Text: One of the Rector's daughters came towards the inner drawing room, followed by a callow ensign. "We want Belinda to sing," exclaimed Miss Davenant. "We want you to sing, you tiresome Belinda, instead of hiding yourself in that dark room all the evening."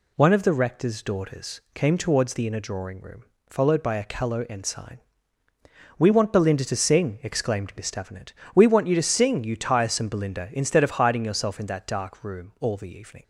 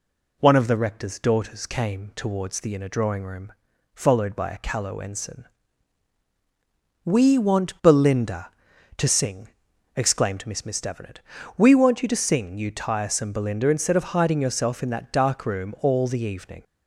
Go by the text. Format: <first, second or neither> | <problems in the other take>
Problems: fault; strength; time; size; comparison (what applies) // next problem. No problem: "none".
first | says "Miss" twice; at 10.6 s